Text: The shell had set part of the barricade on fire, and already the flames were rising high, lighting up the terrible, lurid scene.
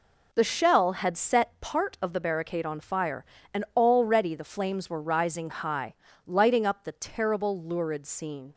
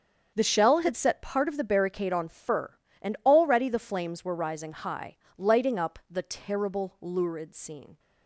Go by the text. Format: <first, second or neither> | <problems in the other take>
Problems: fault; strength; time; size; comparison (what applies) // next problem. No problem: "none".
first | starts louder than the rest; until 1.3 s; 7 dB // says "fur" for "fire"; at 2.2 s